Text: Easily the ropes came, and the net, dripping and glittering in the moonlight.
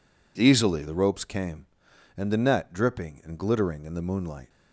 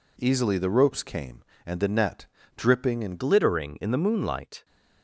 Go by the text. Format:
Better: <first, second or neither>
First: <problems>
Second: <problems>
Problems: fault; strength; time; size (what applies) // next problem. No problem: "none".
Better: first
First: none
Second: changes voice at "glittering"; from 3.1 s on; 1.5 s long